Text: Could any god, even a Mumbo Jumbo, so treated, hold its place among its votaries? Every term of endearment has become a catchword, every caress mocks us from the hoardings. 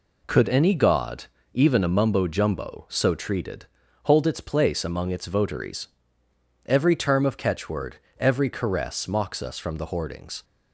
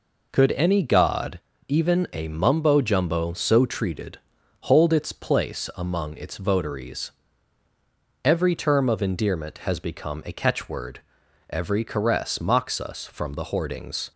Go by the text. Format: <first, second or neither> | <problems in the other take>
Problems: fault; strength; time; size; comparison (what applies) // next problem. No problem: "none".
second | skips "endearment has become a"; at 7.3 s